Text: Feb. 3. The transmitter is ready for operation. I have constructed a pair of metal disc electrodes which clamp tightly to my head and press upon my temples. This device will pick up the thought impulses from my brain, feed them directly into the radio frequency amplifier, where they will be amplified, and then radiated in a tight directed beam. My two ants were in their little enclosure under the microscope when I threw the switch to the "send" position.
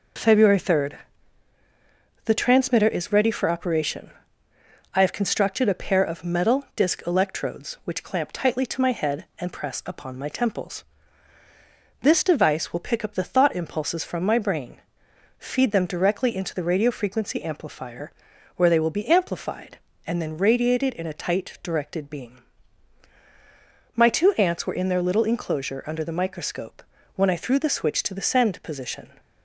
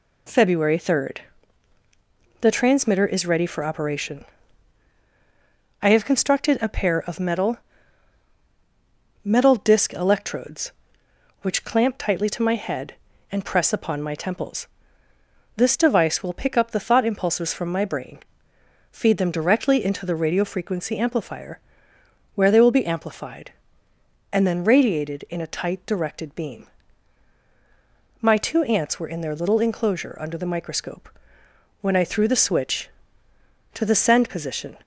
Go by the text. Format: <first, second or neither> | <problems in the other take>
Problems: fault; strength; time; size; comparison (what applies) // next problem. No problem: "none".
first | says "metal" twice; at 9.2 s // pauses between "microscope" and "when"; noticeable; at 31.0 s; 0.74 s long; slight in the first